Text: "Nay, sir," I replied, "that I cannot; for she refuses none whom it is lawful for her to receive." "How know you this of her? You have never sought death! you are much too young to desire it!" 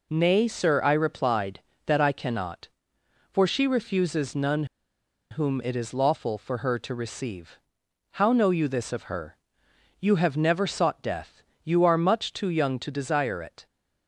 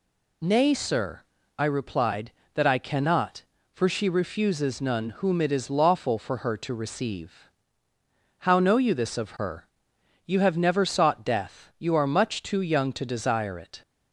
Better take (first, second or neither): second